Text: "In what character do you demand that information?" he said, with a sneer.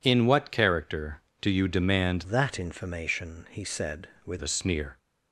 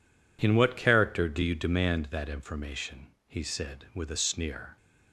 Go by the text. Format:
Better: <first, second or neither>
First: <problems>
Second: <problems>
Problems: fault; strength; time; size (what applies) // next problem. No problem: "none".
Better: second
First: changes voice from "that" to "with"; from 2.2 to 4.3 s; 2.1 s long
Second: none